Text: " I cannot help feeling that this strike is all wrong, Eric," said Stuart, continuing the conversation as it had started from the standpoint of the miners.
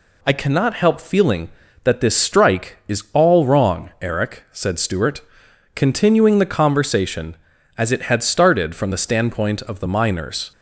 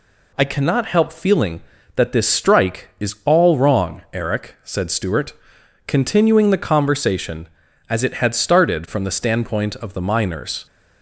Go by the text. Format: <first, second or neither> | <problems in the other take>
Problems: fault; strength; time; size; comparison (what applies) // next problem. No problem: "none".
neither | none